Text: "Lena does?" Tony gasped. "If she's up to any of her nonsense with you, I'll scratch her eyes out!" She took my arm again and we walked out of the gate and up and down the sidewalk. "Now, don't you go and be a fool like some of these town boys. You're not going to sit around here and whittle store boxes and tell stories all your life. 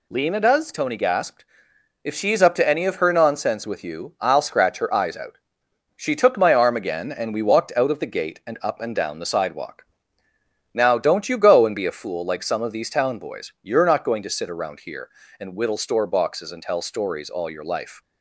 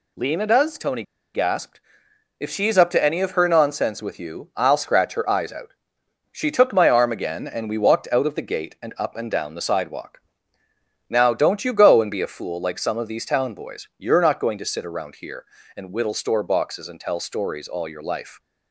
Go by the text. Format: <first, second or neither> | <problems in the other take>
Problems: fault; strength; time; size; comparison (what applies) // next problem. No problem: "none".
first | pauses between "Tony" and "gasped"; slight; at 1.0 s; 0.32 s long